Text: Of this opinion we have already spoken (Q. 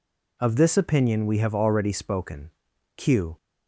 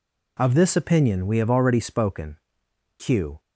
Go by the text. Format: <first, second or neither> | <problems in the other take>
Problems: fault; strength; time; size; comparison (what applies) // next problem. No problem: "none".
neither | none